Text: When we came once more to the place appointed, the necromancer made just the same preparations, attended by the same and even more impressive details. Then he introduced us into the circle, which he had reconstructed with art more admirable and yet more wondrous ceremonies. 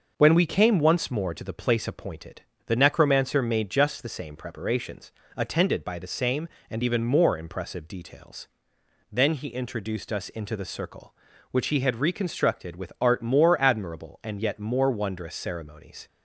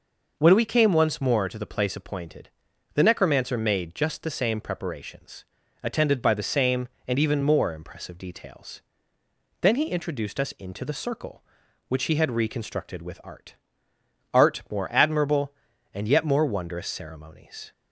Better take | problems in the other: first | says "art" twice; at 14.3 s

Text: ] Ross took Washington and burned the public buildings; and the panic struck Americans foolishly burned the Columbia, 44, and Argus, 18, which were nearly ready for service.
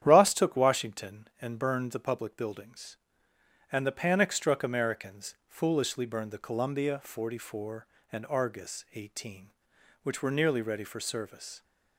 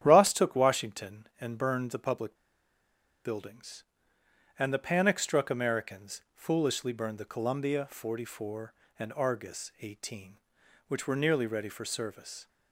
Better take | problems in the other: first | starts louder than the rest; strong; until 1.0 s; 10 dB; strong in the first // pauses between "public" and "buildings"; noticeable; at 2.3 s; 0.90 s long

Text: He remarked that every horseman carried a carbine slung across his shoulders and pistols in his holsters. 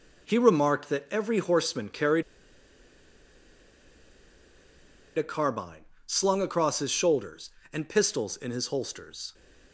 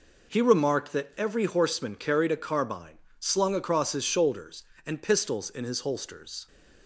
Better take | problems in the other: second | pauses between "carried" and "a"; strong; at 2.2 s; 2.9 s long // pauses between "carbine" and "slung"; slight; at 5.8 s; 0.22 s long; slight in the second

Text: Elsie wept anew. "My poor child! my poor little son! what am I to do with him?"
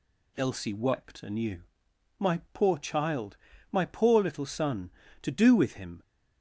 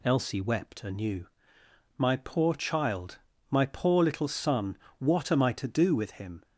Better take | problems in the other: second | skips "what am I"; at 5.0 s

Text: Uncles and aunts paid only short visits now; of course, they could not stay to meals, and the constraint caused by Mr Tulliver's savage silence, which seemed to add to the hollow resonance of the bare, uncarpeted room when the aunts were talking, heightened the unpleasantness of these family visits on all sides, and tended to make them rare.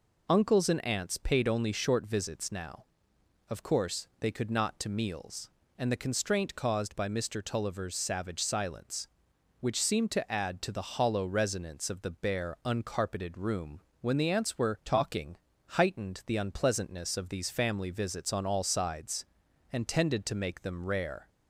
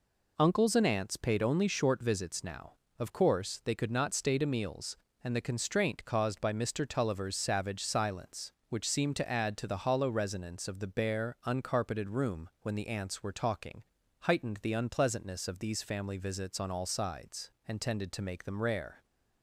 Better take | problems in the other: second | skips "stay"; at 4.7 s // pauses between "room" and "when"; slight; at 13.8 s; 0.18 s long

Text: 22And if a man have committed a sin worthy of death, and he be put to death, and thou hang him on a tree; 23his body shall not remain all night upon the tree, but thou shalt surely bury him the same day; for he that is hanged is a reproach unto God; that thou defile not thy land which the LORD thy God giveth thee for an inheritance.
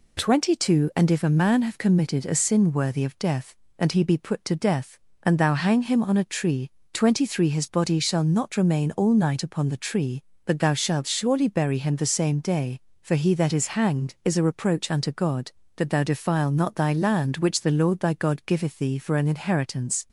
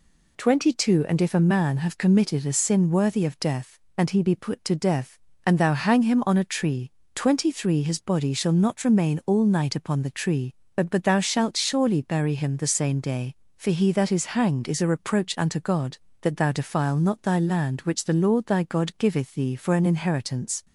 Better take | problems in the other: first | says "but" twice; at 10.9 s

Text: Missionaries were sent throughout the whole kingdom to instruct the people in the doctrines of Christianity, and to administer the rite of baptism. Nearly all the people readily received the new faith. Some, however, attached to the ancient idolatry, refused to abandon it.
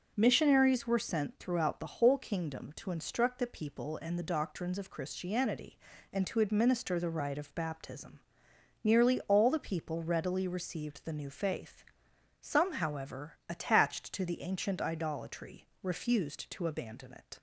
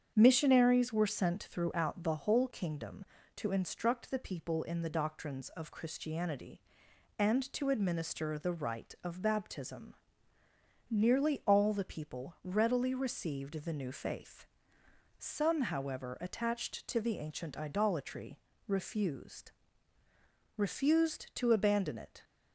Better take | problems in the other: first | starts louder than the rest; strong; until 1.1 s; 8 dB // says "refused" twice; at 20.5 s

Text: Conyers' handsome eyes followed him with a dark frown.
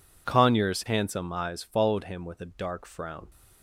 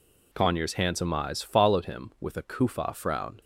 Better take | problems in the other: first | says "kufa" for "dark"; at 2.4 s

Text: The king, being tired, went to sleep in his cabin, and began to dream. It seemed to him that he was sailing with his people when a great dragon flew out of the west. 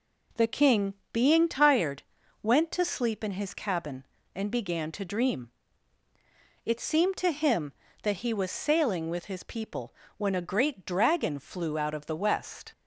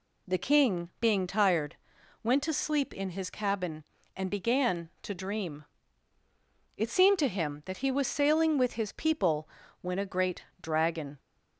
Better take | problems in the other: first | pauses between "people" and "when"; slight; at 9.4 s; 0.34 s long; slight in the first // pauses between "great" and "dragon"; slight; at 10.4 s; 0.18 s long // stops before "flew out of the west"; at 11.1 s

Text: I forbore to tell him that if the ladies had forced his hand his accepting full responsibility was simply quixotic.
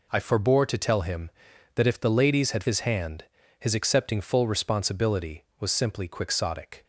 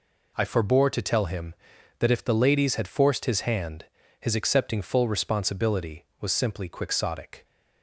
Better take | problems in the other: second | skips "forced"; at 2.6 s // pauses between "hand" and "his"; slight; at 3.2 s; 0.34 s long; slight in the second

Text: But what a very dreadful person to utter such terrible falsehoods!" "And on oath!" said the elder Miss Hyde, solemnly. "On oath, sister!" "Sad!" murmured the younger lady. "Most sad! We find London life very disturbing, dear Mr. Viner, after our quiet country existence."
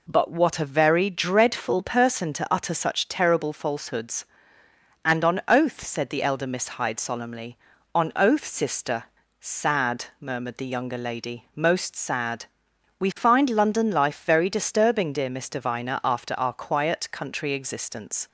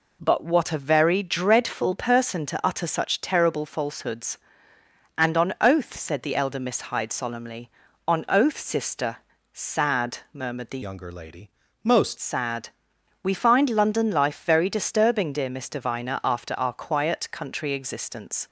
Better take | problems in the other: first | changes voice from "younger" to "Most"; from 10.8 to 12.1 s; 1.3 s long

